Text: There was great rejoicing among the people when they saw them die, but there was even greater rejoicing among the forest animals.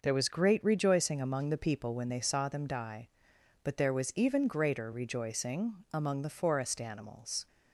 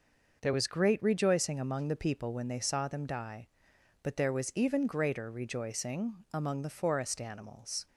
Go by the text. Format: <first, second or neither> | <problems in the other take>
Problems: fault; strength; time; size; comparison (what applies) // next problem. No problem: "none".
neither | none